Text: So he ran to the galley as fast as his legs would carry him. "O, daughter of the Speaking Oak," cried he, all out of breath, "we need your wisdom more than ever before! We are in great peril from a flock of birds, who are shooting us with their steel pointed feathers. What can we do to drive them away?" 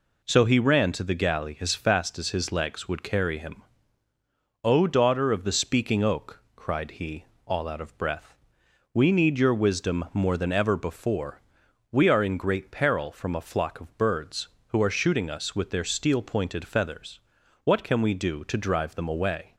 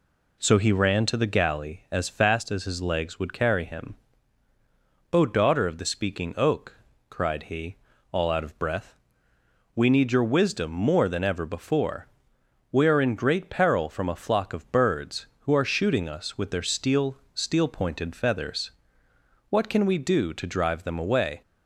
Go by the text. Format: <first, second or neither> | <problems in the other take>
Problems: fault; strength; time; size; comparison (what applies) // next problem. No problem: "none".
first | says "steel" twice; at 17.3 s